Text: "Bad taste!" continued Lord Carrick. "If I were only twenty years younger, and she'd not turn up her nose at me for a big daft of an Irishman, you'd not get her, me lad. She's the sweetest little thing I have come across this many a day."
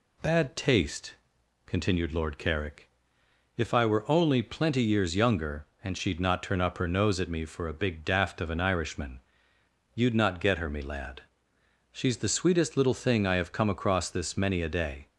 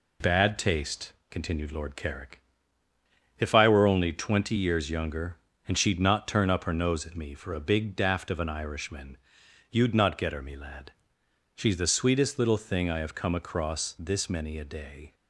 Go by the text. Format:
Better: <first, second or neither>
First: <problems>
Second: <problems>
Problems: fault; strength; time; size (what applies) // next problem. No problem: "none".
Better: second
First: says "plenty" for "twenty"; at 4.4 s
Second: none